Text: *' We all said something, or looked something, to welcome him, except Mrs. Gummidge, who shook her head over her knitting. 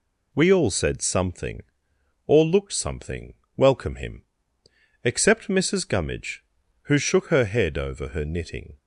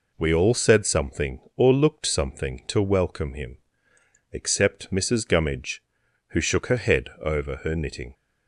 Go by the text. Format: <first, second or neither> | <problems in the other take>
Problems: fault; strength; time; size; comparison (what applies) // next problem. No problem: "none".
second | skips "to"; at 3.4 s